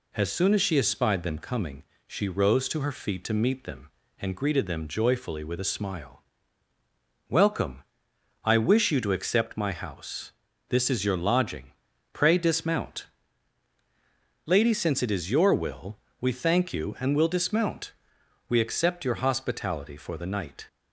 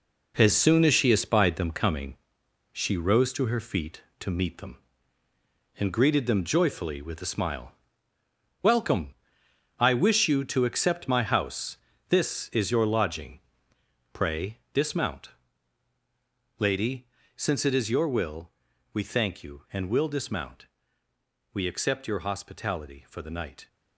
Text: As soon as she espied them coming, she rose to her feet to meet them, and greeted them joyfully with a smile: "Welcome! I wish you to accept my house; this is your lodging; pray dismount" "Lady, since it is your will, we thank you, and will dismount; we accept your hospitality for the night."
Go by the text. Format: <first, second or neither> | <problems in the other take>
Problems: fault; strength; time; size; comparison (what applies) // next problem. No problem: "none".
first | gets quieter; strong; throughout; 8.5 dB // pauses between "pray" and "dismount"; slight; at 14.5 s; 0.16 s long // pauses between "dismount" and "Lady"; strong; at 15.2 s; 1.3 s long; strong in the first